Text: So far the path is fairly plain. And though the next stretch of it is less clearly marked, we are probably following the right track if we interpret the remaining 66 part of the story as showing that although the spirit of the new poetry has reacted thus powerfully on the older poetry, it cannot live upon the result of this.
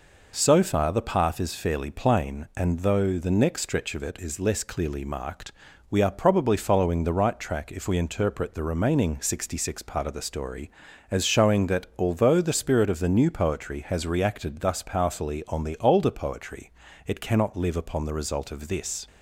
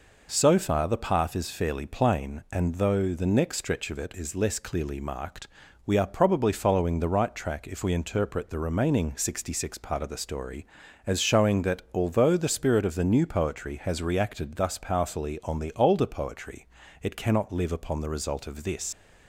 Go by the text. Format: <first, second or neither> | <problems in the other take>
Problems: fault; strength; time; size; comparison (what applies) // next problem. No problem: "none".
first | leaves "this" unfinished; at 18.9 s; 90 ms